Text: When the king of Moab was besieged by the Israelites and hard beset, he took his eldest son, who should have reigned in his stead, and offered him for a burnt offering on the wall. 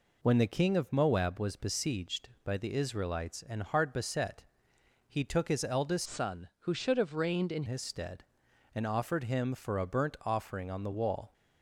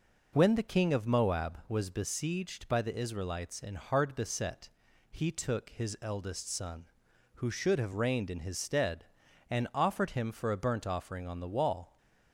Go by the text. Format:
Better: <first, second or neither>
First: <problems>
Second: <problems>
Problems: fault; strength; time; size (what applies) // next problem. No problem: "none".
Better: second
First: changes voice from "son" to "in"; from 6.0 to 7.6 s; 1.6 s long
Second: none